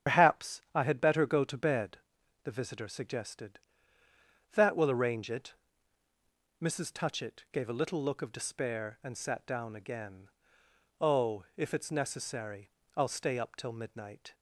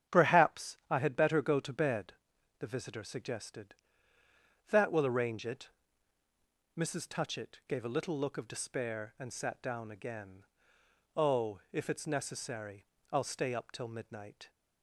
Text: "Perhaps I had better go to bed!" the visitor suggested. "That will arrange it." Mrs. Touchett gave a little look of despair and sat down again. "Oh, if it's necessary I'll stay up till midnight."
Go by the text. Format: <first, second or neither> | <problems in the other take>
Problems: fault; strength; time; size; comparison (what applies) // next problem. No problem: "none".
second | loses the start of "Perhaps"; at 0.0 s; 125 ms // starts louder than the rest; strong; until 1.1 s; 8.5 dB; strong in the second // pauses between "necessary" and "I'll"; slight; at 12.6 s; 0.26 s long; slight in the second